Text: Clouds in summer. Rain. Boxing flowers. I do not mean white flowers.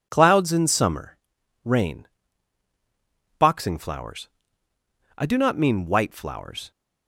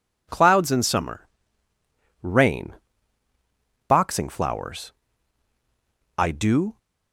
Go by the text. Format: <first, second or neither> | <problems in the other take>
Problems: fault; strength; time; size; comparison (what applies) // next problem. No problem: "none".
first | stops before "not mean white flowers"; at 6.7 s